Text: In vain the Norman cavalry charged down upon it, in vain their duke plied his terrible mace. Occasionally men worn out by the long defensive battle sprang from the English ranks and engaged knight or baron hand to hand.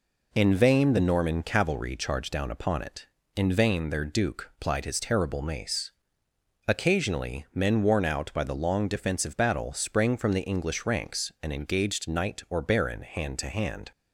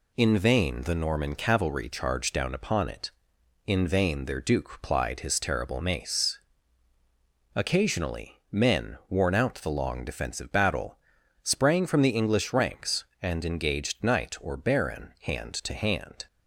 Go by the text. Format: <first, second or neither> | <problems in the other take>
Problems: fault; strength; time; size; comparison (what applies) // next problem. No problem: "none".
first | skips "by"; at 9.5 s // pauses between "battle" and "sprang"; noticeable; at 10.9 s; 0.46 s long